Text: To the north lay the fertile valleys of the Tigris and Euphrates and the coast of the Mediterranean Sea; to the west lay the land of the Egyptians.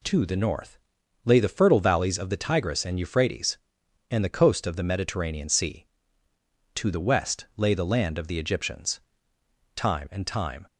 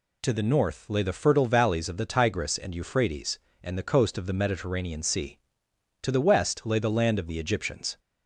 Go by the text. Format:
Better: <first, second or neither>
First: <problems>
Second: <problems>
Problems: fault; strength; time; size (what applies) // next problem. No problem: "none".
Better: second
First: pauses between "north" and "lay"; noticeable; at 0.7 s; 0.46 s long // goes on to say "Time and time"; noticeable; from 9.7 s on; 0.90 s long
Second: none